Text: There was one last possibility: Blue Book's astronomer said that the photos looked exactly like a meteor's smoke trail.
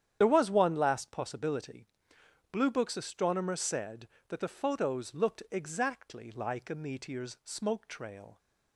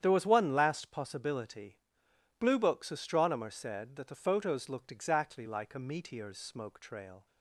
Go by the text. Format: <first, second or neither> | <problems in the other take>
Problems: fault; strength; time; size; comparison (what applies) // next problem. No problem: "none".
second | loses the start of "There"; at 0.2 s; 35 ms // starts louder than the rest; strong; until 1.2 s; 9.5 dB; strong in the second